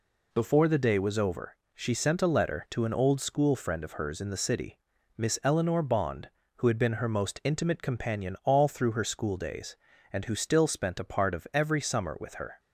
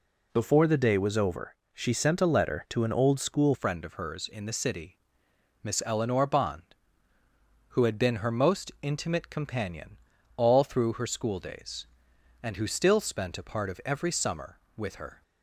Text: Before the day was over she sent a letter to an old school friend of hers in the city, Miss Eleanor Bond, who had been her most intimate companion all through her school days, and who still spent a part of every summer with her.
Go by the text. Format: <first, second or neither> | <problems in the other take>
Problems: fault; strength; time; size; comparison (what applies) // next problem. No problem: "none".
first | pauses between "over" and "she"; slight; at 1.5 s; 0.18 s long; slight in the first // changes voice at "friend"; from 3.5 s on; 11.7 s long // pauses between "companion" and "all"; at 9.9 s; 0.40 s long